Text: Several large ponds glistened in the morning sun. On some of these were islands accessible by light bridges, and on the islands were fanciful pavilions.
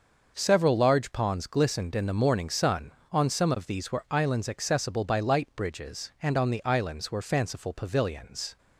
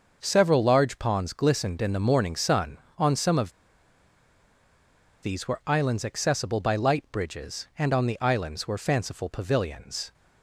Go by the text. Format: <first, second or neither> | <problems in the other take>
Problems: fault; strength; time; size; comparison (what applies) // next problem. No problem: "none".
first | starts louder than the rest; until 1.2 s; 6 dB; also in the first // pauses between "of" and "these"; strong; at 3.5 s; 1.7 s long